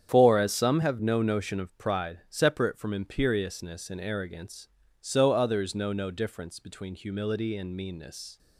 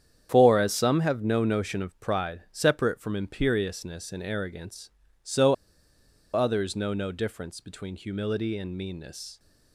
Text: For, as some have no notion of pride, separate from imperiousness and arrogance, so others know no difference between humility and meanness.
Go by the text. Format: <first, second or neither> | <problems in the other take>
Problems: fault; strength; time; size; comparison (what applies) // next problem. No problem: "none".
first | starts louder than the rest; strong; until 1.3 s; 8.5 dB; strong in the first // pauses between "so" and "others"; noticeable; at 5.5 s; 0.79 s long